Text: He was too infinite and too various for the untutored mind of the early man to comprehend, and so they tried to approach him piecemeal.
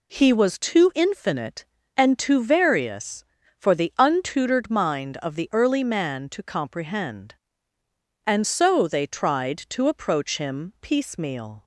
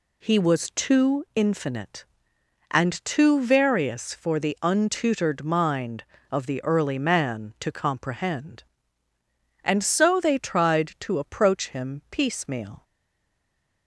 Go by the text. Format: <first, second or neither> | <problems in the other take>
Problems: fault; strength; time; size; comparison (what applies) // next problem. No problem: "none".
first | stays silent after the last word; from 12.8 s on; 1.0 s long